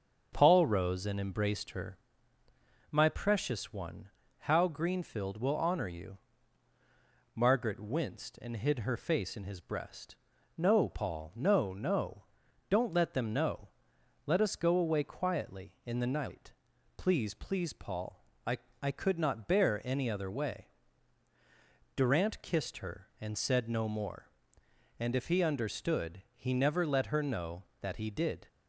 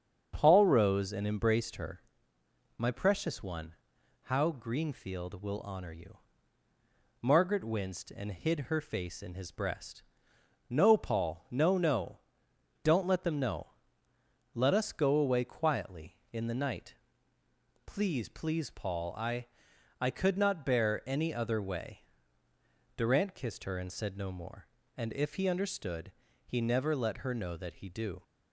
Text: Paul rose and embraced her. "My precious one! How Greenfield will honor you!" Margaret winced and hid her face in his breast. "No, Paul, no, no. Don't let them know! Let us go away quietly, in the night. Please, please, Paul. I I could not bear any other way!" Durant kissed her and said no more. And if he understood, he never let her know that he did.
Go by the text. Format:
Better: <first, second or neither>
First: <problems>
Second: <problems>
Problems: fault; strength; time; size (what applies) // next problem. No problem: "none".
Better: first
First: starts louder than the rest; until 1.3 s; 6.5 dB // pauses between "I" and "I"; slight; at 18.5 s; 0.24 s long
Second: starts louder than the rest; strong; until 1.3 s; 7 dB // pauses between "I" and "I"; noticeable; at 19.4 s; 0.56 s long // says "do" for "did"; at 27.8 s